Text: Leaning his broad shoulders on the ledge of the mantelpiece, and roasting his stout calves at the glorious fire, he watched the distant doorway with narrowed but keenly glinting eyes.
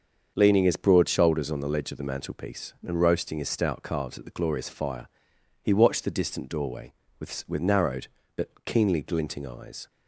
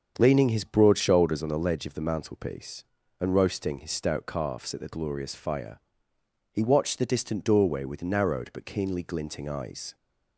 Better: second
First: starts louder than the rest; until 1.3 s; 6.5 dB // says "with" twice; at 7.4 s // pauses between "but" and "keenly"; slight; at 8.4 s; 0.16 s long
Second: starts louder than the rest; until 1.1 s; 7 dB

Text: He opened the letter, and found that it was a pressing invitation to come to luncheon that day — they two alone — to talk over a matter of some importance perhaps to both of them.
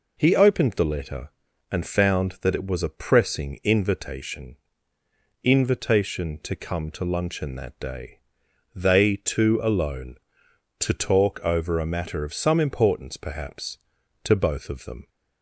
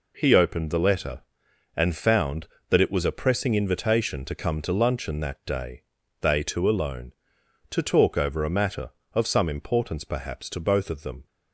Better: second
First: says "invitation" twice; at 5.4 s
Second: none

